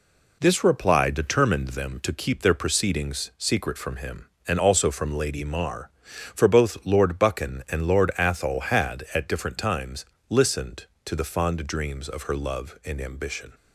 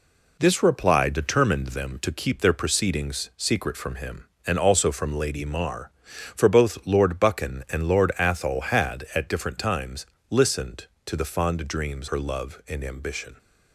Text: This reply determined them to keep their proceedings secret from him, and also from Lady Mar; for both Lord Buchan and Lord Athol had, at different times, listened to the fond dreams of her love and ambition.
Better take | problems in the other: first | skips "of"; at 12.0 s

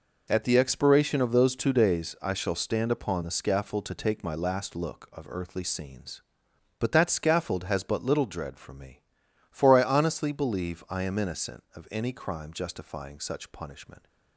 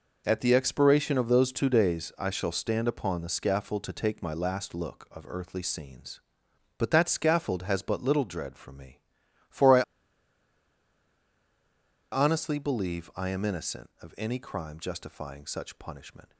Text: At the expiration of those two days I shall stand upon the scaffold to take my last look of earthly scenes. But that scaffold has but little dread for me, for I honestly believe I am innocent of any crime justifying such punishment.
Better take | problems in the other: first | pauses between "I" and "honestly"; strong; at 9.8 s; 2.3 s long

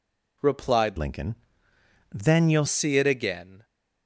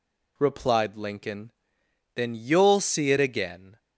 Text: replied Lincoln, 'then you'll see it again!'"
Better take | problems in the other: second | changes voice from "Lincoln" to "you'll"; from 0.9 to 2.6 s; 1.7 s long

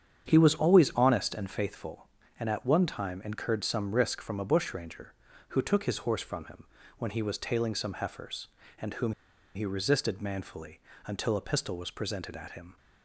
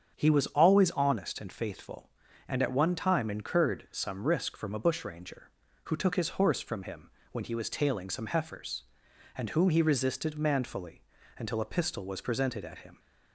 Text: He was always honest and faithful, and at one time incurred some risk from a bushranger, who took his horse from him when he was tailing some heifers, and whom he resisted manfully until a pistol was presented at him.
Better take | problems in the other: second | starts louder than the rest; strong; until 1.2 s; 8 dB; strong in the second // pauses between "him" and "when"; slight; at 6.6 s; 0.34 s long; slight in the second // pauses between "whom" and "he"; at 9.1 s; 0.42 s long // pauses between "manfully" and "until"; slight; at 10.8 s; 0.26 s long; slight in the second

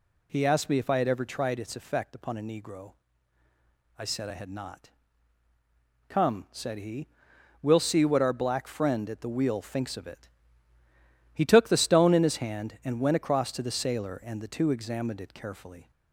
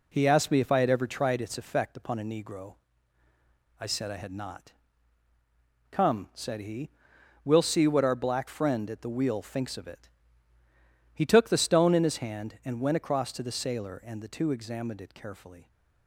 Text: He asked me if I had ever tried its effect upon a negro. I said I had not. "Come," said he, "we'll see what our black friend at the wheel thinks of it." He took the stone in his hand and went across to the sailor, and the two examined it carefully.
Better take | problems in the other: first | gets quieter; noticeable; throughout; 5.5 dB

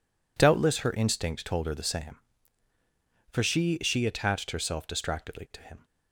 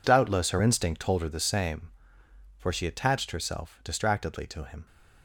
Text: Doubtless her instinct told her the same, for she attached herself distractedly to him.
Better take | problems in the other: second | says "she" twice; at 3.8 s

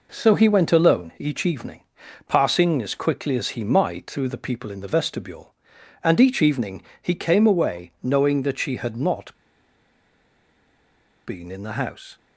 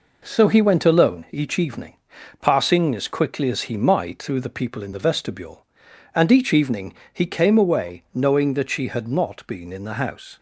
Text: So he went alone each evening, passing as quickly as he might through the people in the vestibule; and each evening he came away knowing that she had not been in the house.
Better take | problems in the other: second | pauses between "evening" and "he"; slight; at 6.8 s; 0.18 s long; slight in the second // pauses between "not" and "been"; strong; at 9.3 s; 1.9 s long

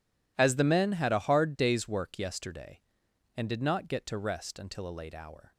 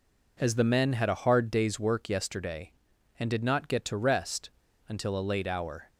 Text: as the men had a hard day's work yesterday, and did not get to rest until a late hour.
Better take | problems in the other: first | pauses between "rest" and "until"; at 4.5 s; 0.38 s long

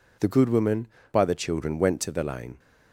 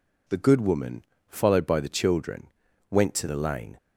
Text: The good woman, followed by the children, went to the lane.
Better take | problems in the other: second | skips "followed"; at 1.0 s

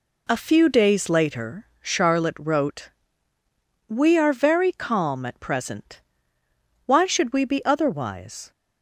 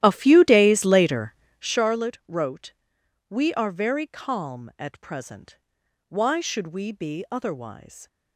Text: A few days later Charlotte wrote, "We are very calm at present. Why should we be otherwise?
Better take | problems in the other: first | starts louder than the rest; strong; until 1.8 s; 13 dB // pauses between "later" and "Charlotte"; slight; at 1.3 s; 0.26 s long

